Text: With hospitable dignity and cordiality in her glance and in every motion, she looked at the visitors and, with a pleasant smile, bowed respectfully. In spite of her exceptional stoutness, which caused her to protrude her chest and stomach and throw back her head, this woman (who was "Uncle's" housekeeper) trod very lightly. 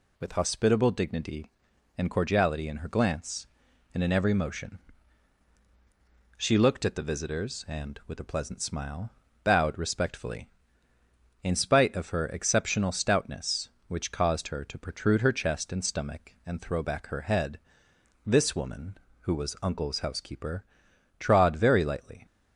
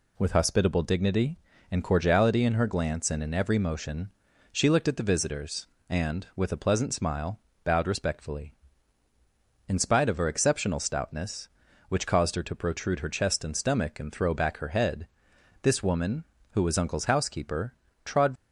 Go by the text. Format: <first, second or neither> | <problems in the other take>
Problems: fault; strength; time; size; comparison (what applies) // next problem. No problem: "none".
first | stops before "very lightly"; at 18.3 s